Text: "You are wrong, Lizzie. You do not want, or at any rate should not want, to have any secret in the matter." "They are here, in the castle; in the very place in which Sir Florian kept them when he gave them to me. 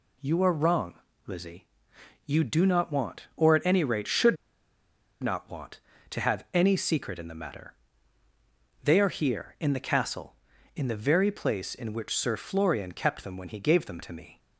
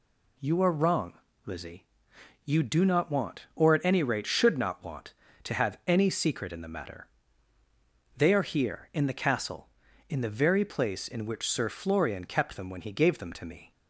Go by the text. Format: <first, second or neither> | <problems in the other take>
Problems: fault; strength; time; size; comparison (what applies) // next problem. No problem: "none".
second | pauses between "should" and "not"; noticeable; at 4.3 s; 0.86 s long